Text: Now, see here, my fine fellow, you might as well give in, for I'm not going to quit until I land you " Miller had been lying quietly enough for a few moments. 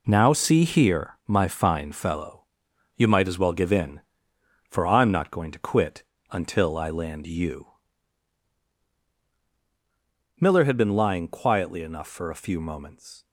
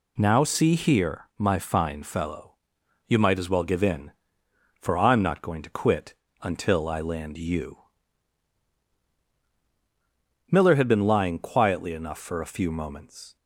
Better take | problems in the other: second | gets quieter; strong; throughout; 20 dB // pauses between "quit" and "until"; slight; at 6.0 s; 0.28 s long; slight in the second

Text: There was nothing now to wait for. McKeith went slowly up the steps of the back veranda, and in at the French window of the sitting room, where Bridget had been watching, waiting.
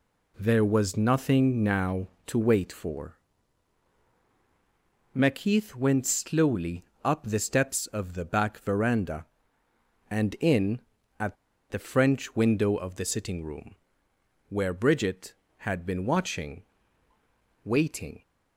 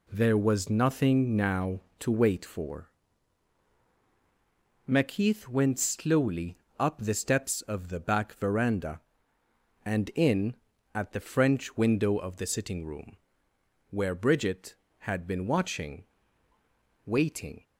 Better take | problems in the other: second | pauses between "slowly" and "up"; slight; at 6.8 s; 0.20 s long; slight in the second // pauses between "at" and "the"; slight; at 11.3 s; 0.35 s long

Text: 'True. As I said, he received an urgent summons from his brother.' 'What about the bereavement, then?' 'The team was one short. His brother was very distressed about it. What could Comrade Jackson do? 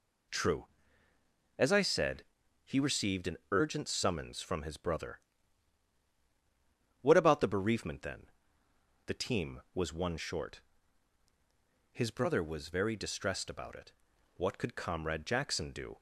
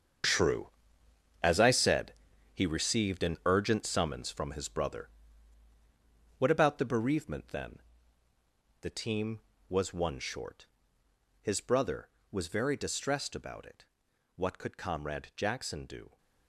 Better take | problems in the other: first | gets quieter; strong; throughout; 12.5 dB

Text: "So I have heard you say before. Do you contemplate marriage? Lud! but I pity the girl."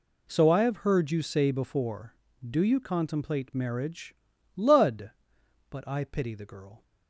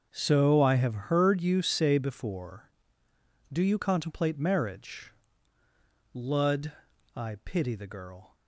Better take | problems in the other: first | starts louder than the rest; until 1.1 s; 6.5 dB // skips "but"; at 6.9 s

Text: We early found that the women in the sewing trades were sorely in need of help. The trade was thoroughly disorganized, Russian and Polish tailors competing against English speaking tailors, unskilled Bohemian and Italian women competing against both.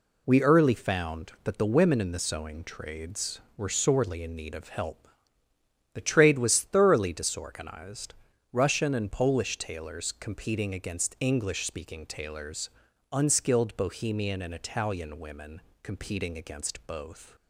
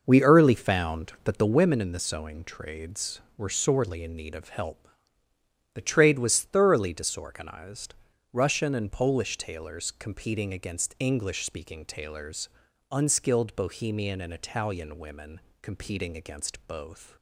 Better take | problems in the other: first | starts louder than the rest; noticeable; until 1.6 s; 6 dB // pauses between "women" and "competing"; slight; at 15.3 s; 0.22 s long; slight in the first

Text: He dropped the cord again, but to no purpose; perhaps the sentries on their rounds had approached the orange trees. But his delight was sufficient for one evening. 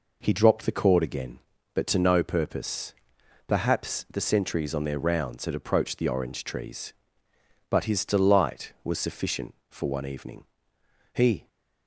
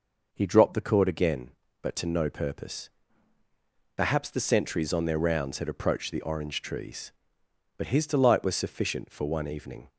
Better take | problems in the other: second | goes on to say "He"; slight; from 11.1 s on; 0.36 s long

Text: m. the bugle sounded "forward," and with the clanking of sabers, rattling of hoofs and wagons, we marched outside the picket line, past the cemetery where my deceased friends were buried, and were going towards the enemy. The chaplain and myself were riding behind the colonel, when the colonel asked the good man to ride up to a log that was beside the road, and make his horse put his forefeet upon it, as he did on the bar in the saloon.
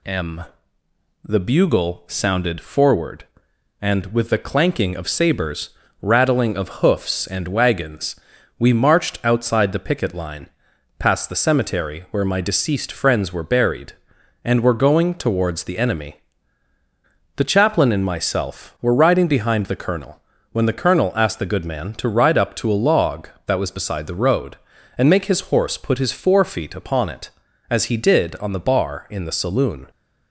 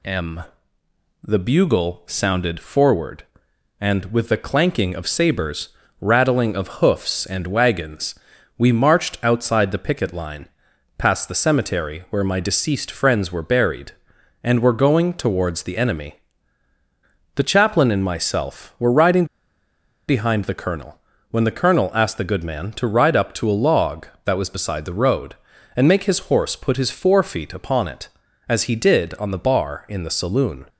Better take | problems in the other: first | pauses between "riding" and "behind"; noticeable; at 19.2 s; 0.82 s long

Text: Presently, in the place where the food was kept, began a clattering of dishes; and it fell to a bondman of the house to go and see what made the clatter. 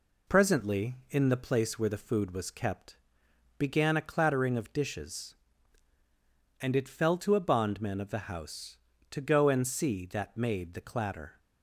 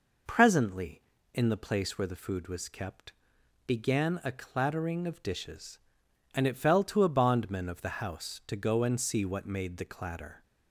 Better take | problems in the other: second | says "that" for "what"; at 10.0 s

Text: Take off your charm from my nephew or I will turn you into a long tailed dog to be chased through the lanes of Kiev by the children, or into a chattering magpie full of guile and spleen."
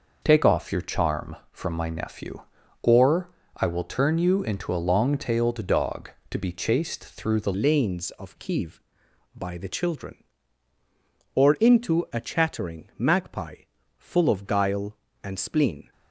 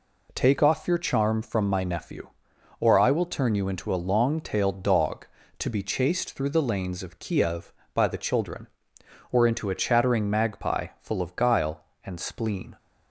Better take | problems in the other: second | pauses between "or" and "I"; slight; at 3.2 s; 0.28 s long // changes voice at "lanes"; from 7.5 s on; 8.4 s long // pauses between "magpie" and "full"; slight; at 13.6 s; 0.36 s long

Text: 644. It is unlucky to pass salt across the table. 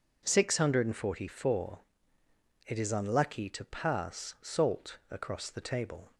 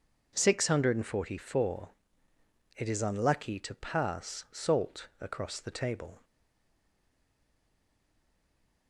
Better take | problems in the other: first | pauses between "salt" and "across"; slight; at 5.0 s; 0.16 s long; slight in the first // stays silent after the last word; strong; from 6.2 s on; 2.6 s long

